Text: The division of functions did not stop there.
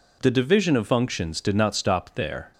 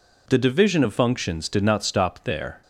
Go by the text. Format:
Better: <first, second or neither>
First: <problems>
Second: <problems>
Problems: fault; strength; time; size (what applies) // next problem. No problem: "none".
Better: neither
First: none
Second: none